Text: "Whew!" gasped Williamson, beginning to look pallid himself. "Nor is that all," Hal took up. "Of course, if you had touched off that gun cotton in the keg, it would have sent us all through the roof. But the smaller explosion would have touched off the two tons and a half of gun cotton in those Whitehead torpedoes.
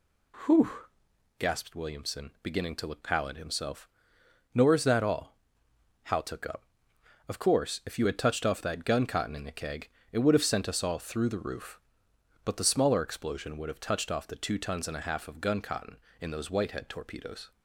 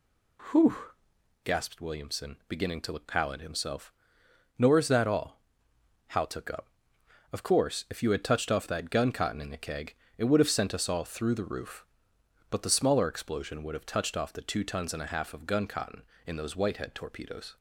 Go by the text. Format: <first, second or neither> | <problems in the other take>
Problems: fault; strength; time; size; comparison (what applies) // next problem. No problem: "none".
neither | none